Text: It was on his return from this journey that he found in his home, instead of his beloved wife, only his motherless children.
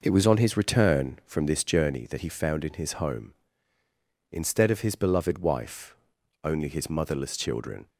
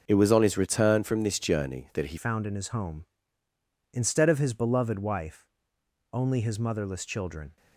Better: first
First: none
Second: changes voice at "found"; from 2.1 s on; 5.4 s long

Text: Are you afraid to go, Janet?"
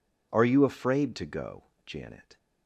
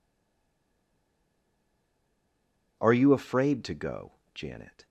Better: first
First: none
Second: stays silent before the first word; strong; until 2.7 s; 2.7 s long

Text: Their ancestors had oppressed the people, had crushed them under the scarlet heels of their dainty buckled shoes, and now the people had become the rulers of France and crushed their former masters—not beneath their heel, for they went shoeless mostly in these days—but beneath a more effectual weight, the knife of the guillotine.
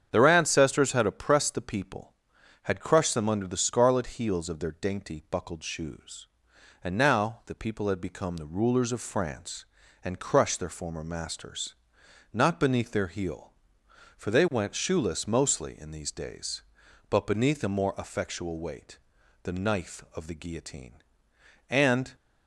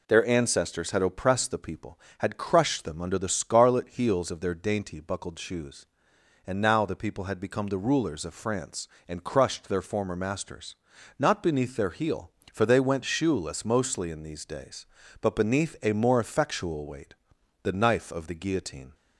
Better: second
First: starts louder than the rest; strong; until 1.1 s; 8 dB // goes on to say "And"; slight; from 21.6 s on; 0.44 s long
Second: none

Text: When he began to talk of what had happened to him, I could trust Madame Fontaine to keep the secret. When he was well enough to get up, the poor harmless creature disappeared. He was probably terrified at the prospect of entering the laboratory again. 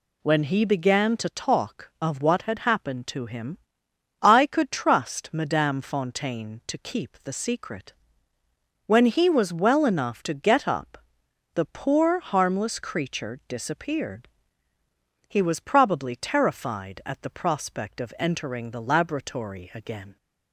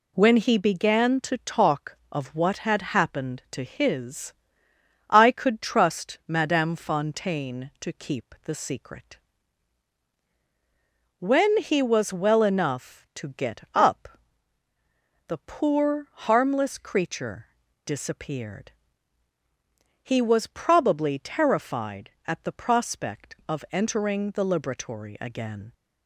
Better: first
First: none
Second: says "his" for "him"; at 3.6 s // pauses between "creature" and "disappeared"; at 17.4 s; 0.40 s long

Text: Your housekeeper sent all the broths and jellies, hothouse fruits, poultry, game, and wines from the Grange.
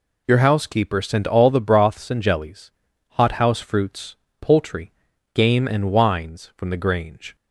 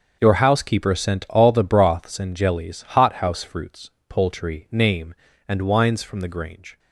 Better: first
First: none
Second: starts louder than the rest; until 1.2 s; 6.5 dB // says "name" for "game"; at 4.6 s

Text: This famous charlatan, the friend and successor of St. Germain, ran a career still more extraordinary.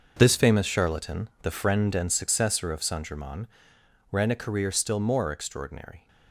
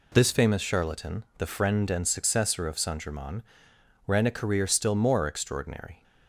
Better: second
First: gets quieter; strong; throughout; 11.5 dB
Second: none

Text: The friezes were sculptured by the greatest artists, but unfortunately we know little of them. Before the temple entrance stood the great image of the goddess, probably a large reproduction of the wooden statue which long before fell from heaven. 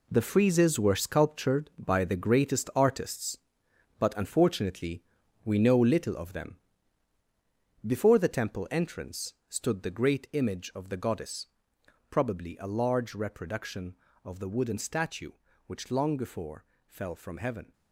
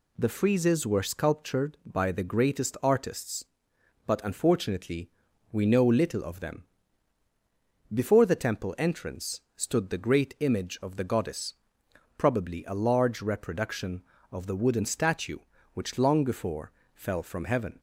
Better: second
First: gets quieter; strong; throughout; 10.5 dB // pauses between "unfortunately" and "we"; at 5.0 s; 0.42 s long // pauses between "before" and "fell"; slight; at 16.6 s; 0.22 s long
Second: pauses between "unfortunately" and "we"; at 5.0 s; 0.42 s long // pauses between "before" and "fell"; slight; at 16.7 s; 0.22 s long

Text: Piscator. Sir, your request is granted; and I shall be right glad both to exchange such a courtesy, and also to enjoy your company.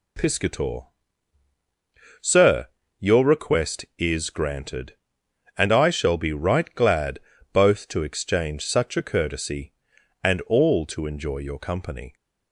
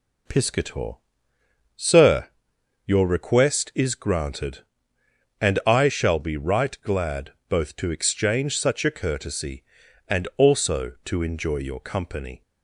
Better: second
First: pauses between "glad" and "both"; slight; at 7.1 s; 0.34 s long // says "all" for "also"; at 10.4 s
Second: pauses between "glad" and "both"; slight; at 7.3 s; 0.16 s long

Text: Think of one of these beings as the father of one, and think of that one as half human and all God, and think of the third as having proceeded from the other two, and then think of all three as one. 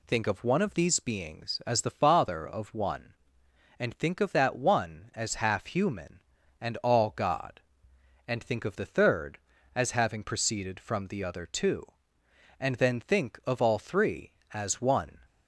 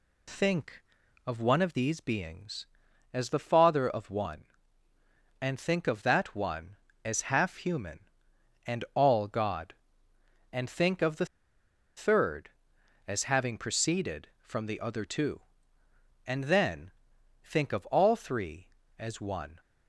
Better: first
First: none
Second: pauses between "the" and "third"; noticeable; at 11.2 s; 0.72 s long // pauses between "then" and "think"; noticeable; at 16.8 s; 0.54 s long

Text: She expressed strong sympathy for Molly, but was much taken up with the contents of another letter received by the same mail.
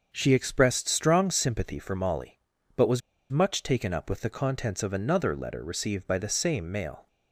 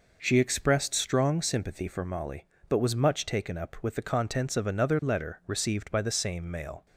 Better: second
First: starts louder than the rest; until 1.1 s; 7 dB // pauses between "was" and "much"; slight; at 3.0 s; 0.30 s long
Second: none

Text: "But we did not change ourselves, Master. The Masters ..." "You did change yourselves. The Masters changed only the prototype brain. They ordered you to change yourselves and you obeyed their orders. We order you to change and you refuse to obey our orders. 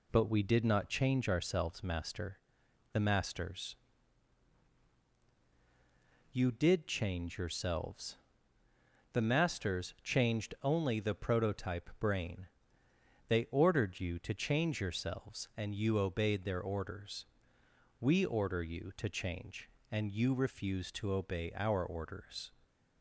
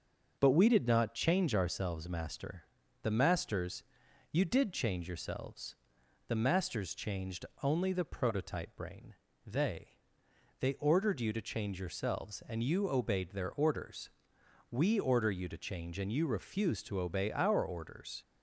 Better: first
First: none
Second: starts louder than the rest; until 1.4 s; 6.5 dB // pauses between "changed" and "only"; slight; at 7.4 s; 0.20 s long // says "They" twice; at 10.5 s

